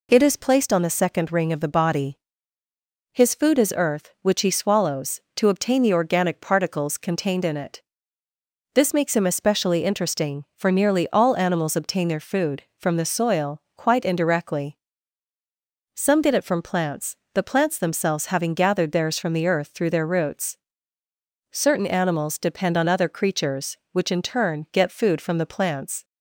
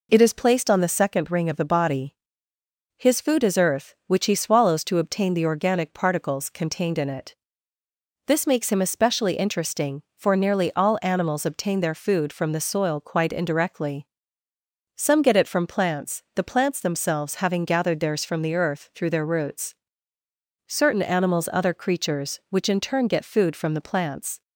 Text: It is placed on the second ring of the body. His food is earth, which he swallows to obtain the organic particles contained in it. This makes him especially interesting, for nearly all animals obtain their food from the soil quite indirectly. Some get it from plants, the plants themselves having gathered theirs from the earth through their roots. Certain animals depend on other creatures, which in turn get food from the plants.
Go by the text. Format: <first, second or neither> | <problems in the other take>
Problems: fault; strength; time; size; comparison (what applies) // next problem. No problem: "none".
first | skips "depend on"; at 21.5 s